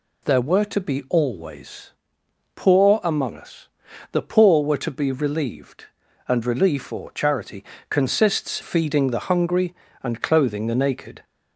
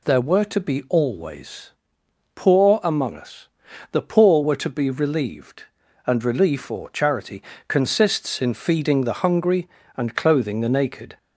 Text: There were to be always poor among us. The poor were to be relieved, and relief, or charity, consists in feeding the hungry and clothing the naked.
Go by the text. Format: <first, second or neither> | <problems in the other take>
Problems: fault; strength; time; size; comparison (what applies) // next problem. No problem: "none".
second | pauses between "always" and "poor"; noticeable; at 1.9 s; 0.64 s long; noticeable in the second // skips "in"; at 8.6 s